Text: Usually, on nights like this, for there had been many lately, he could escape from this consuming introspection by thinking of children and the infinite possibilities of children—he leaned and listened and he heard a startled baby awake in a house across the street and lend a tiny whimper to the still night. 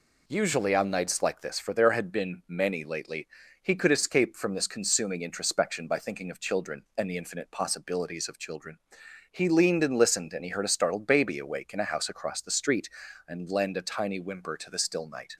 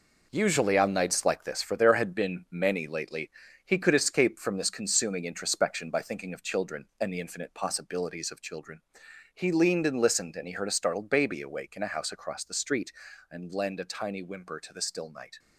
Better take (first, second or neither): first